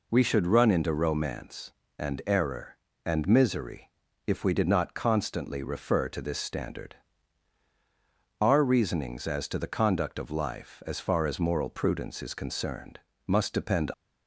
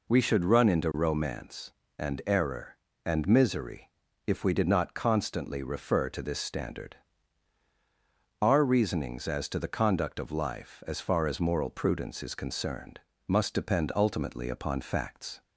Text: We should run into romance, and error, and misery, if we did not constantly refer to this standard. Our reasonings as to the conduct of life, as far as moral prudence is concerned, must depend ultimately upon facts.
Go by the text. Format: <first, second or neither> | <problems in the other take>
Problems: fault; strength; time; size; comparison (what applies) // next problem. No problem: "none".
second | stops before "ultimately upon facts"; at 13.9 s